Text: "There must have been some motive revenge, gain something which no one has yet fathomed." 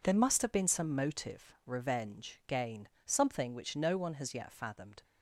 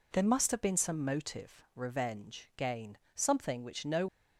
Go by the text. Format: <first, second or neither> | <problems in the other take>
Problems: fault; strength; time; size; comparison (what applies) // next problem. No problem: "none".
first | pauses between "gain" and "something"; slight; at 2.9 s; 0.18 s long; slight in the first // stops before "one has yet fathomed"; at 4.0 s